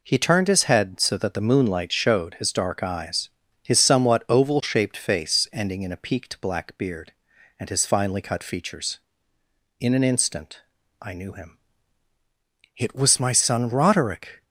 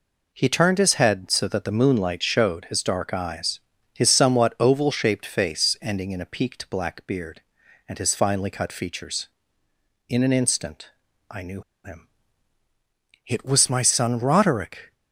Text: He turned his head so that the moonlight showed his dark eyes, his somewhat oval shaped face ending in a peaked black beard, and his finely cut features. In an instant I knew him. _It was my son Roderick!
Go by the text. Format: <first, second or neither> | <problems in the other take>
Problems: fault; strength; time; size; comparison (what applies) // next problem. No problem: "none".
first | pauses between "instant" and "I"; at 10.9 s; 0.38 s long; also in the first // pauses between "knew" and "him"; slight; at 11.6 s; 0.23 s long